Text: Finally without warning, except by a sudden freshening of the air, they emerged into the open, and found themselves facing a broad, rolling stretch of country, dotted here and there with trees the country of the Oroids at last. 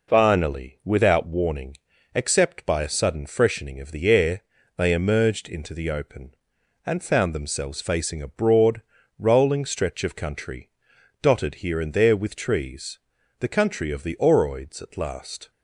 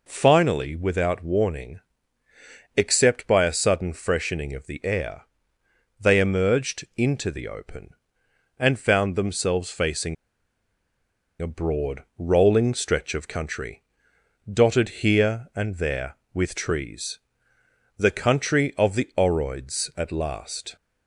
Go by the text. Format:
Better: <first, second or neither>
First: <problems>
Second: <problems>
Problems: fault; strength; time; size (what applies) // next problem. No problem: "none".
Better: first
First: pauses between "trees" and "the"; at 12.9 s; 0.40 s long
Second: pauses between "facing" and "a"; strong; at 10.1 s; 1.2 s long // pauses between "trees" and "the"; noticeable; at 17.1 s; 0.78 s long